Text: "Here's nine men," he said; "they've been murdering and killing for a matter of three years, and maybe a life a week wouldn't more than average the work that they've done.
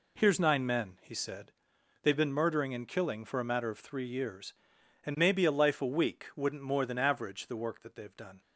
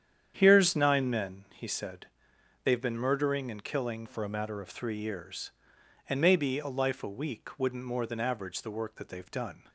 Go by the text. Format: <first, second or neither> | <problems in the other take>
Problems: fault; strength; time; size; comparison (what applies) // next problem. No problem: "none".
first | starts louder than the rest; strong; until 1.3 s; 9 dB // changes voice from "for" to "of"; from 4.0 to 4.6 s; 0.6 s long